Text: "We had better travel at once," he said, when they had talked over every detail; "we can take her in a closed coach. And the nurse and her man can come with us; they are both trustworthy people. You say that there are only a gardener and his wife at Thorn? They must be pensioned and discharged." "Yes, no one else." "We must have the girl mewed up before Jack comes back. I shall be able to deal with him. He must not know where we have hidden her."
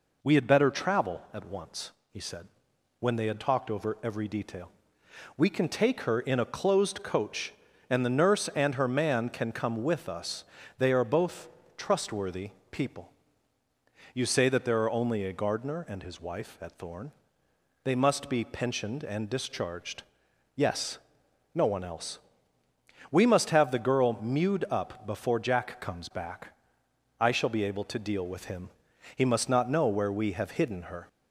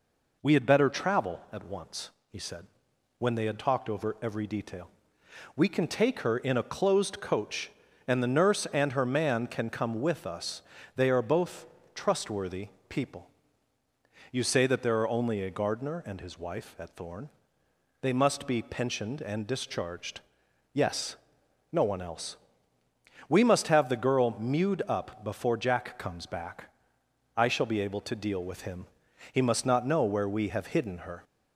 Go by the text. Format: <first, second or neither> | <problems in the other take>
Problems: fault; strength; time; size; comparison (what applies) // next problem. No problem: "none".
neither | pauses between "both" and "trustworthy"; slight; the same in both // pauses between "trustworthy" and "people"; slight; the same in both